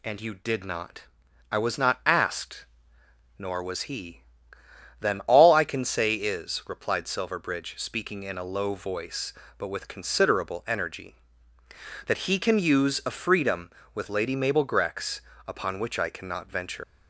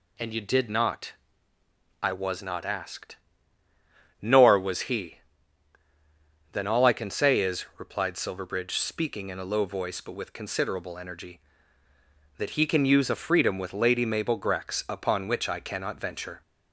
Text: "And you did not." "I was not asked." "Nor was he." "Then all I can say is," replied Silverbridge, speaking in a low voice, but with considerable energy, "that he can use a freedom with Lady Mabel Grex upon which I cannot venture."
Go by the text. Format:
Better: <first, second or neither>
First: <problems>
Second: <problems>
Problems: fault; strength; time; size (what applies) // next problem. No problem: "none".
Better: second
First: pauses between "Grex" and "upon"; slight; at 15.2 s; 0.26 s long // leaves "venture" unfinished; at 16.8 s; 110 ms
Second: none